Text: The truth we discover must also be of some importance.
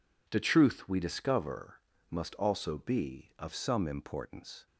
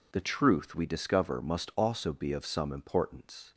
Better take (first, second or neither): second